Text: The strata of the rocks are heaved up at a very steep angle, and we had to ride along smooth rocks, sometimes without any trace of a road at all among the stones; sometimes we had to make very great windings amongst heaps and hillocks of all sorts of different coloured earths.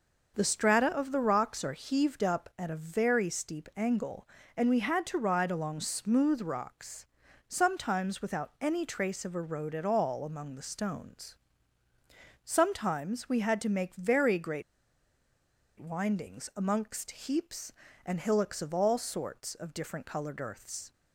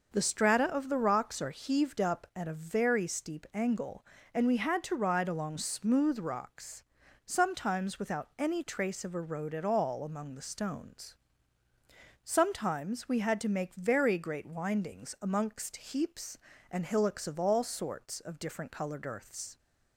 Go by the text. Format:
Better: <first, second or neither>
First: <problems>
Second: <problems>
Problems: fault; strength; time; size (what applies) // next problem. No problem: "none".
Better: second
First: pauses between "great" and "windings"; at 14.6 s; 1.1 s long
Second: none